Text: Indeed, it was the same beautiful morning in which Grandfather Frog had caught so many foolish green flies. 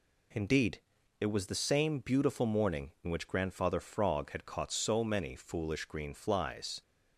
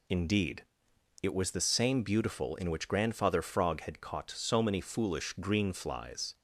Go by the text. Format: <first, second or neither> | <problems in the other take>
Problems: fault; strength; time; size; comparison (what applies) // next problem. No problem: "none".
first | skips "morning"; at 2.5 s